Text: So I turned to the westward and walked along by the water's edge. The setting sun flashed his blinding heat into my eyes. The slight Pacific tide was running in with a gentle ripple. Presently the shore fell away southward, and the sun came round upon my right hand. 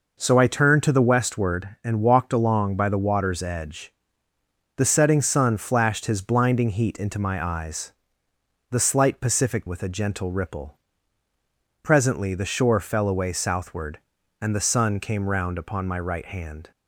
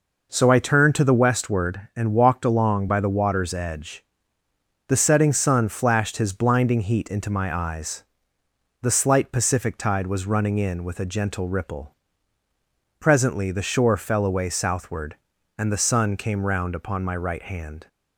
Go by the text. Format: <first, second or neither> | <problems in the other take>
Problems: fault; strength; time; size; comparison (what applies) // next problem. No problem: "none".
second | skips "tide was running in"; at 9.6 s